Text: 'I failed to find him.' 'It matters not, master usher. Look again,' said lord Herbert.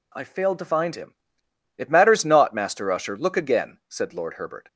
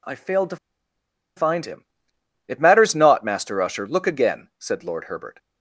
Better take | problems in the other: first | pauses between "to" and "find"; noticeable; at 0.5 s; 0.80 s long

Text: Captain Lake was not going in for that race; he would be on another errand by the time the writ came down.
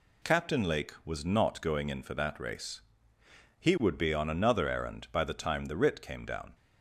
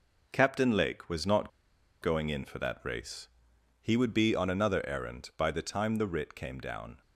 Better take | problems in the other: first | pauses between "not" and "going"; noticeable; at 1.4 s; 0.52 s long

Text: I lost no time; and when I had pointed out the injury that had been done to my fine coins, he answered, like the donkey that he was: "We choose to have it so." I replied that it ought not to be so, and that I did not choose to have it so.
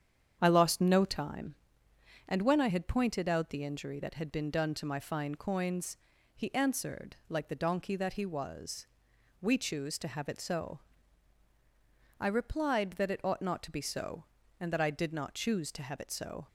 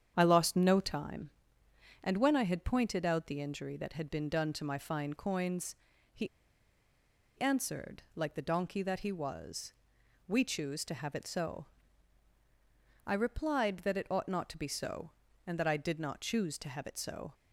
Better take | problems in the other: first | starts louder than the rest; strong; until 1.1 s; 8.5 dB; strong in the first // pauses between "he" and "answered"; at 6.2 s; 1.1 s long

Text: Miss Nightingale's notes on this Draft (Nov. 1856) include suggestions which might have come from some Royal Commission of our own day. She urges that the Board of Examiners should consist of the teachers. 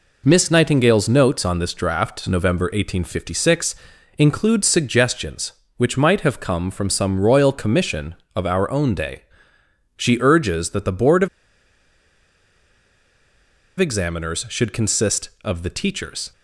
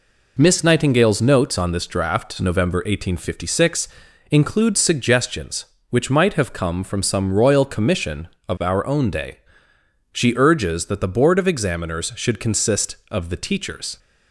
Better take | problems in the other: second | pauses between "of" and "Examiners"; strong; at 11.2 s; 2.5 s long

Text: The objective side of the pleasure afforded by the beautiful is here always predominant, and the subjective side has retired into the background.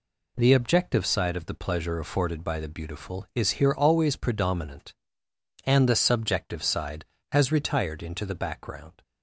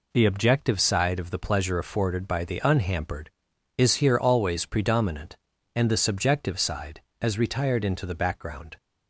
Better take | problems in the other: first | says "unhampered" for "beautiful"; at 2.6 s

